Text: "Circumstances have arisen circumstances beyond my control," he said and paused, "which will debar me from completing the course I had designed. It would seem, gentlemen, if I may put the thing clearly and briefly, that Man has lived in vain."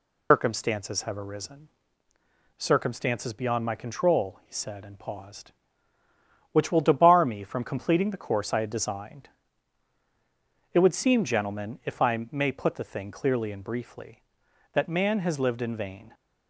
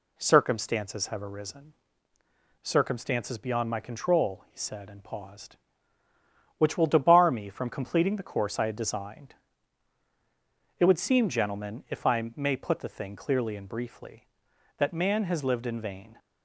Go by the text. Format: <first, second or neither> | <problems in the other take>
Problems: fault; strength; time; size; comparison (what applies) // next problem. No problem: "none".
second | loses the start of "Circumstances"; at 0.3 s; 165 ms // pauses between "arisen" and "circumstances"; noticeable; at 1.6 s; 0.88 s long; noticeable in the second